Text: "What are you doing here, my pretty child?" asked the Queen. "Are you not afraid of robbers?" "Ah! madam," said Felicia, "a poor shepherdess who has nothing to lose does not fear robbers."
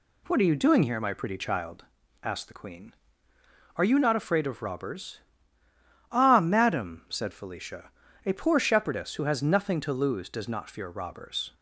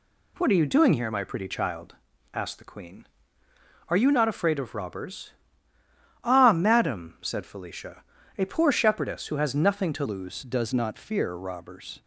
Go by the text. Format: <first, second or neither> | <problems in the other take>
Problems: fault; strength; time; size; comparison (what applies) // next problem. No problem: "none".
first | changes voice at "lose"; from 10.0 s on; 2.0 s long